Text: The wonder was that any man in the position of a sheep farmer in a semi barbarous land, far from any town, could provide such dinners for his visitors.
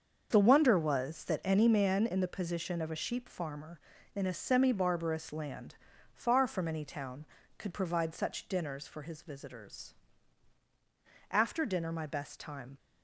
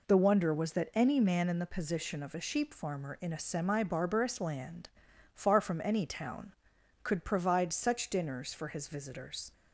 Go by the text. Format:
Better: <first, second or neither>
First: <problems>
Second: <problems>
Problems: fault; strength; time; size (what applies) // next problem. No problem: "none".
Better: second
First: starts louder than the rest; until 1.3 s; 6.5 dB // goes on to say "After dinner my best time"; from 11.3 s on; 1.4 s long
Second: none